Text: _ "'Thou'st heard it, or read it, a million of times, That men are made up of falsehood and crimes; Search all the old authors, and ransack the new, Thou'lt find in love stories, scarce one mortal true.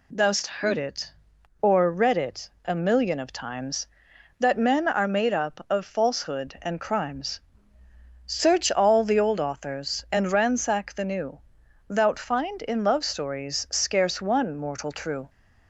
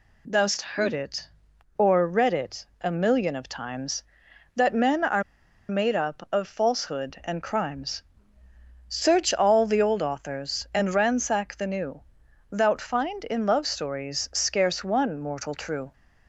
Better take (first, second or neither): first